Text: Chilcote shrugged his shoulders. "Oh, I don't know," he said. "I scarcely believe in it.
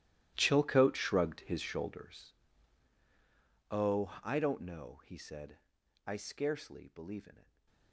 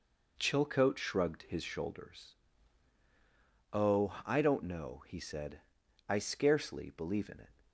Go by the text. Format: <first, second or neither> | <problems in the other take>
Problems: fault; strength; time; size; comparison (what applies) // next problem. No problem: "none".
second | gets quieter; strong; throughout; 21 dB // stays silent after the last word; slight; from 7.4 s on; 0.5 s long